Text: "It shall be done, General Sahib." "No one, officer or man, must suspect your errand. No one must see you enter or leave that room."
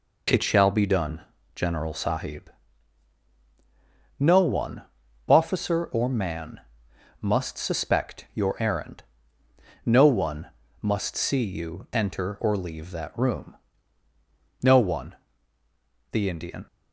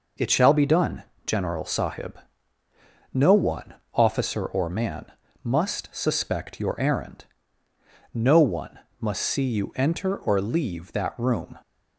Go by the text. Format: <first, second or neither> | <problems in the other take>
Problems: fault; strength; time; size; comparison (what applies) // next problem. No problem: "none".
second | pauses between "one" and "must"; slight; at 10.4 s; 0.34 s long; slight in the second // goes on to say "No one the Indian"; strong; from 14.6 s on; 2.0 s long